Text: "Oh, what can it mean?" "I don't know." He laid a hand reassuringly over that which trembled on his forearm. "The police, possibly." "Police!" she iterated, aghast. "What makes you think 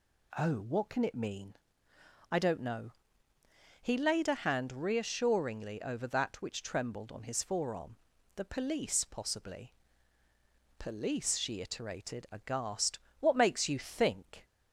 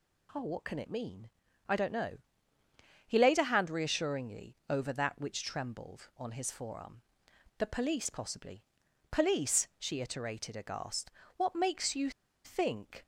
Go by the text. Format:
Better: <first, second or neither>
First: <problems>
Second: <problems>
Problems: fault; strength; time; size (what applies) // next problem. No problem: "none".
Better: first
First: none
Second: pauses between "you" and "think"; slight; at 12.1 s; 0.34 s long